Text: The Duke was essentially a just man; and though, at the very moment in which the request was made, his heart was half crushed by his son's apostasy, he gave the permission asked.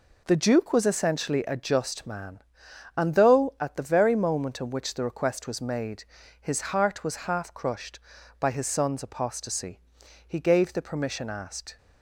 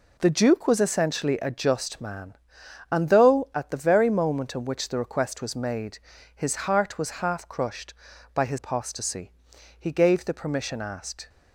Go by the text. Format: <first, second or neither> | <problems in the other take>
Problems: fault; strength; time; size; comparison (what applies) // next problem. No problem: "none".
first | skips "son's"; at 8.5 s